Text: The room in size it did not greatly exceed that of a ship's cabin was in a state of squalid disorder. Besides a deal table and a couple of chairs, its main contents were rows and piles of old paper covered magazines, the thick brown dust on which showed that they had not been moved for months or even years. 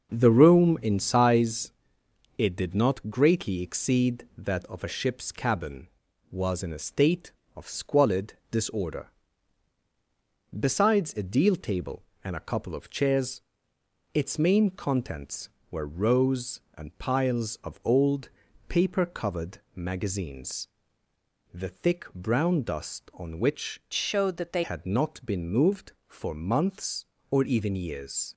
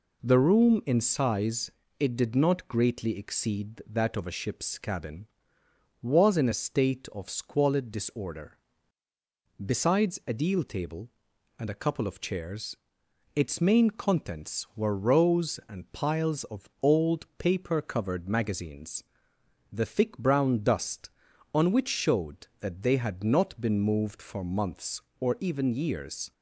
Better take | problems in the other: second | starts louder than the rest; until 1.1 s; 6.5 dB // pauses between "size" and "it"; noticeable; at 1.7 s; 0.66 s long; slight in the second // pauses between "old" and "paper"; at 18.2 s; 0.40 s long // pauses between "covered" and "magazines"; slight; at 19.5 s; 0.18 s long // changes voice from "showed" to "they"; from 23.9 to 24.6 s; 0.7 s long

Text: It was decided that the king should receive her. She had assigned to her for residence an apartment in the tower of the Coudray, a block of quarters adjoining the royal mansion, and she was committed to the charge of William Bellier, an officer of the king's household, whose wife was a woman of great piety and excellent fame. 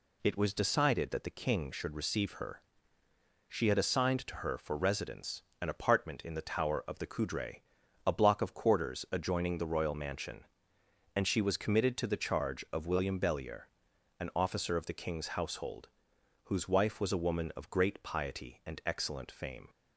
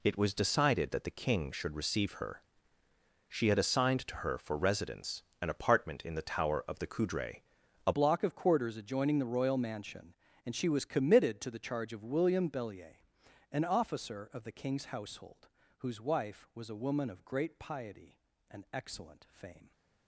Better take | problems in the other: first | pauses between "residence" and "an"; slight; at 5.2 s; 0.20 s long; slight in the first // changes voice at "block"; from 7.9 s on; 11.8 s long

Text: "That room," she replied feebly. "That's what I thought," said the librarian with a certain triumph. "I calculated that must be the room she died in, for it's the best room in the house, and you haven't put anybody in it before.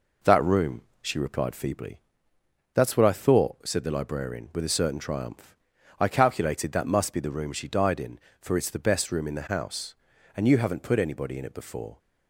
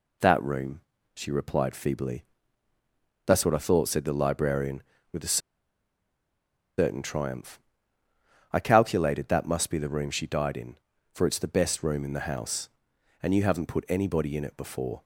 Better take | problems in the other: first | pauses between "a" and "certain"; strong; at 5.3 s; 1.4 s long

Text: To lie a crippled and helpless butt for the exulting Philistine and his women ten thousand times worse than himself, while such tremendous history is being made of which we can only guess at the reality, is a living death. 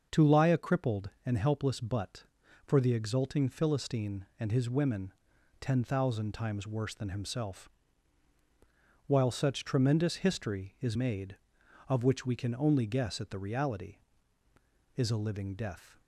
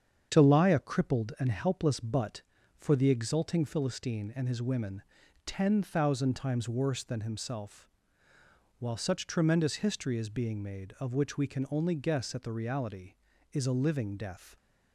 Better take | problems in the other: second | starts louder than the rest; until 1.3 s; 6.5 dB; strong in the second // pauses between "women" and "ten"; noticeable; at 5.1 s; 0.46 s long; also in the second // skips "being"; at 10.9 s

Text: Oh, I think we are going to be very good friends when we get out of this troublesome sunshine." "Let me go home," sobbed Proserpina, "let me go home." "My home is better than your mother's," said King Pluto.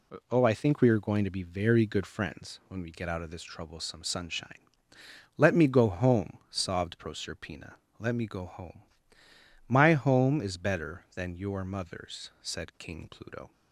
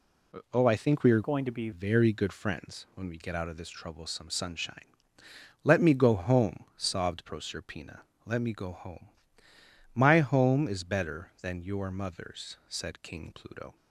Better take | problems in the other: first | changes voice from "going" to "be"; from 1.2 to 1.6 s; 0.4 s long

